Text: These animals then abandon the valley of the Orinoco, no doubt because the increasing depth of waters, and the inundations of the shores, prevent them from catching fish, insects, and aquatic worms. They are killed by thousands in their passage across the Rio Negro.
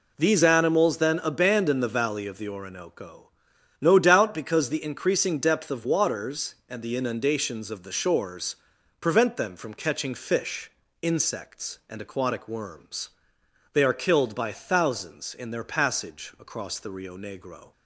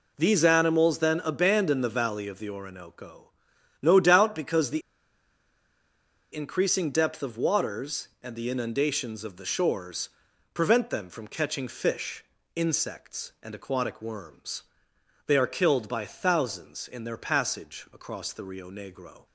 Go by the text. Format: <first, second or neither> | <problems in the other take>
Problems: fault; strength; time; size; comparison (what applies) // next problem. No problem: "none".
first | pauses between "the" and "increasing"; strong; at 4.8 s; 1.5 s long